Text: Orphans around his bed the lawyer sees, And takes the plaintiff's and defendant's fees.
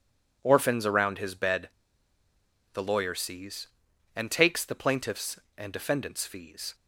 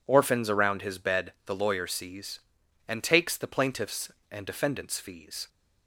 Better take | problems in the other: second | pauses between "bed" and "the"; at 1.6 s; 1.0 s long

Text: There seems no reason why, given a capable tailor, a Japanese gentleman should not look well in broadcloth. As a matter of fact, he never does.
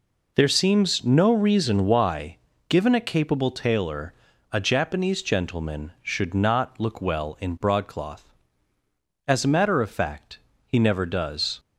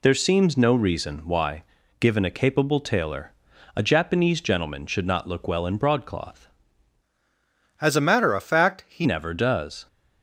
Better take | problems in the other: first | changes voice from "As" to "he"; from 7.8 to 9.0 s; 1.2 s long

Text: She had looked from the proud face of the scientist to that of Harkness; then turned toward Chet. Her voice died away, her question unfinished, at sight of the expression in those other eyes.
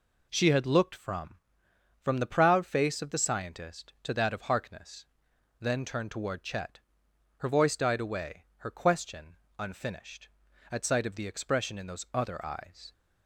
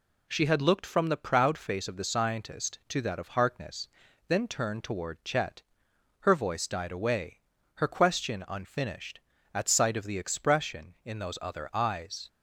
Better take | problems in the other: second | says "from" twice; at 2.0 s // pauses between "question" and "unfinished"; slight; at 9.3 s; 0.24 s long

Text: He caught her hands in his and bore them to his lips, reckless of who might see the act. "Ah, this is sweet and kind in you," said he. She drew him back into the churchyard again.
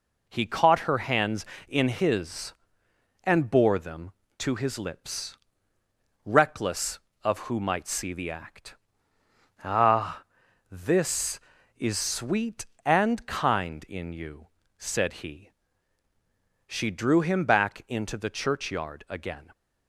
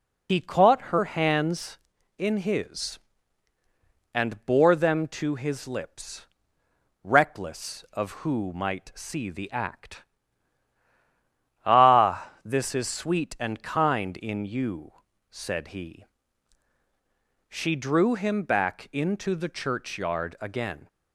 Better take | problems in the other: first | loses the start of "He"; at 0.2 s; 75 ms

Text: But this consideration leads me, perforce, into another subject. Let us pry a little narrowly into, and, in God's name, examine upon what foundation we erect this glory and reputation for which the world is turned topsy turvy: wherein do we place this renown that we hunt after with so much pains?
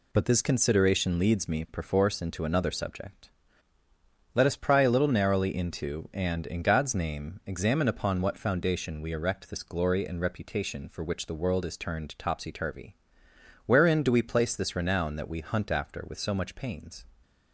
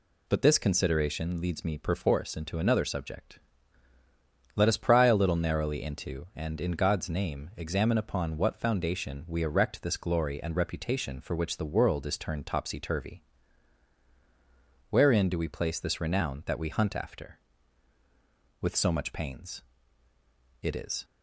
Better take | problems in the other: first | goes on to say "It is"; slight; from 20.6 s on; 0.42 s long

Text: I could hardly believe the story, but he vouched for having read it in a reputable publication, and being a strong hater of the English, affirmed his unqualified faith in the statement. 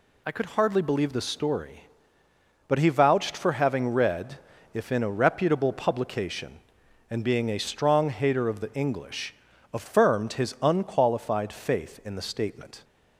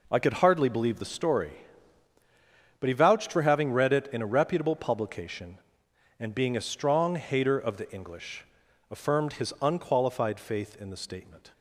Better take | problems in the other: second | says "if" for "it"; at 4.7 s

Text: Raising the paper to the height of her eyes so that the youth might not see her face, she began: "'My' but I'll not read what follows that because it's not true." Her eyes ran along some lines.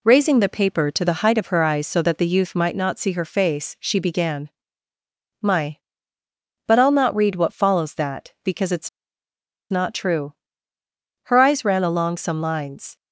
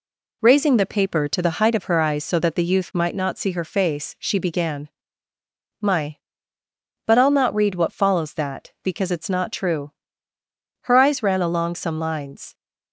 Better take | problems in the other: second | pauses between "it's" and "not"; noticeable; at 8.8 s; 0.82 s long

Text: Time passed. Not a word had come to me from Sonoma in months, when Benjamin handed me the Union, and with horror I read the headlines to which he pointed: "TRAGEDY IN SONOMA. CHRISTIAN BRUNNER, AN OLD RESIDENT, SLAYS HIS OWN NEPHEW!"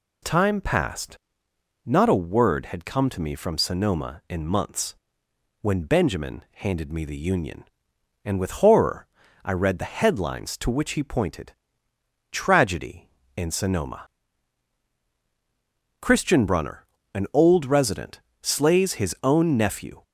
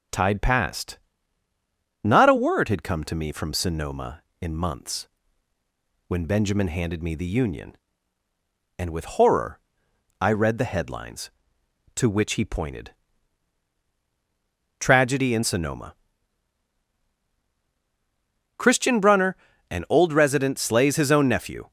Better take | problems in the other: first | says "Tide" for "Time"; at 0.1 s // pauses between "horror" and "I"; noticeable; at 9.5 s; 0.62 s long; also in the first

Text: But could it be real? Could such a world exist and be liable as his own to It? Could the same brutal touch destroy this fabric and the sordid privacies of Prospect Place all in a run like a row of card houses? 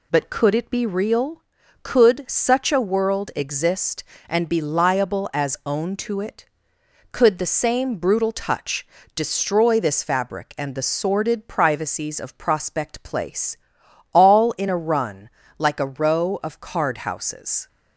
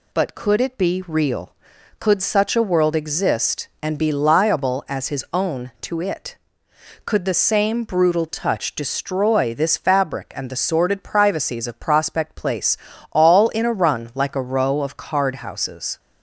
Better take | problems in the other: second | skips "his"; at 5.6 s // pauses between "touch" and "destroy"; slight; at 8.8 s; 0.28 s long // pauses between "Place" and "all"; noticeable; at 13.5 s; 0.56 s long; slight in the second // pauses between "run" and "like"; slight; at 15.2 s; 0.28 s long

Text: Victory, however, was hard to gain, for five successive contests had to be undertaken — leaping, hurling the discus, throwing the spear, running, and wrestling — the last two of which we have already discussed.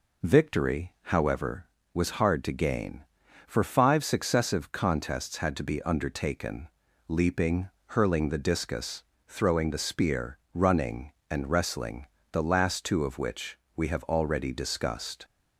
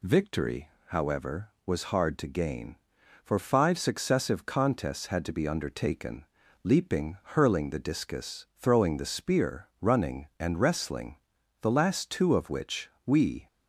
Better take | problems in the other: first | pauses between "which" and "we"; slight; at 12.8 s; 0.18 s long; slight in the first // stops before "have already discussed"; at 13.4 s

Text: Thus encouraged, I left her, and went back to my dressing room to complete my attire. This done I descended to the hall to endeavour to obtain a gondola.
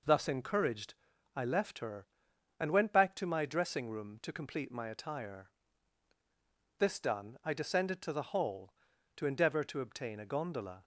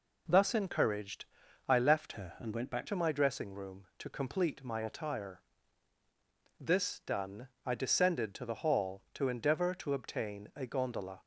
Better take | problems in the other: first | changes voice from "her" to "back"; from 2.1 to 2.8 s; 0.7 s long // pauses between "done" and "I"; slight; at 7.4 s; 0.18 s long

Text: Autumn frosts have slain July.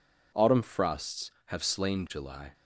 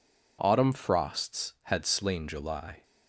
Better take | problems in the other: first | says "had" for "have"; at 1.6 s

